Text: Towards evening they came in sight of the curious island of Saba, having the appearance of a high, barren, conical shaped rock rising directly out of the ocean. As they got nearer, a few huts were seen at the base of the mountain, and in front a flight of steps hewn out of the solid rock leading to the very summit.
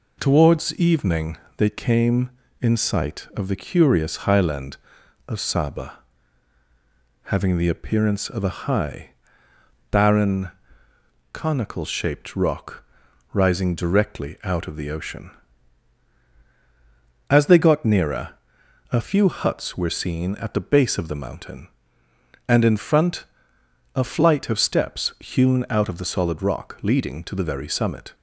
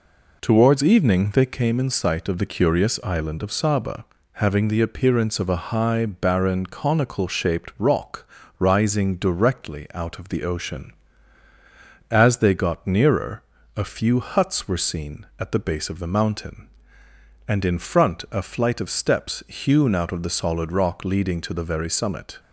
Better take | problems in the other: second | pauses between "evening" and "they"; slight; at 1.3 s; 0.20 s long // says "highland" for "island"; at 4.2 s // pauses between "rock" and "rising"; noticeable; at 12.8 s; 0.50 s long; slight in the second // pauses between "front" and "a"; noticeable; at 23.2 s; 0.72 s long

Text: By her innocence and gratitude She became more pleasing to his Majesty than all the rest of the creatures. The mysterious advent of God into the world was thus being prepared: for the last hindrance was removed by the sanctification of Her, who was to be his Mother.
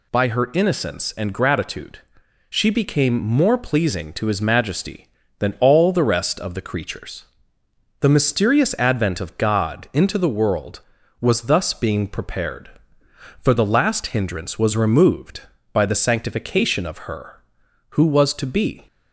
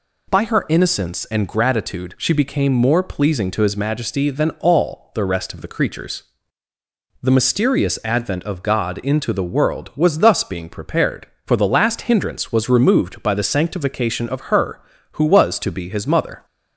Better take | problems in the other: second | pauses between "gratitude" and "She"; noticeable; at 1.9 s; 0.50 s long // stops before "his Mother"; at 18.8 s

